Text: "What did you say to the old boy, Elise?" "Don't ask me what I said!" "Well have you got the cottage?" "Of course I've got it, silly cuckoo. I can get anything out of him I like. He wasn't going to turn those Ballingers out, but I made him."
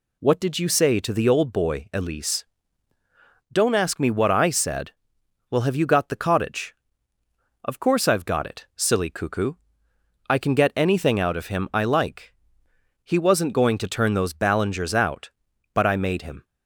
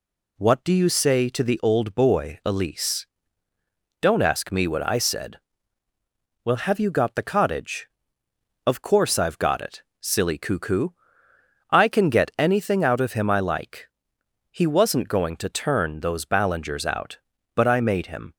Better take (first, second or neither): first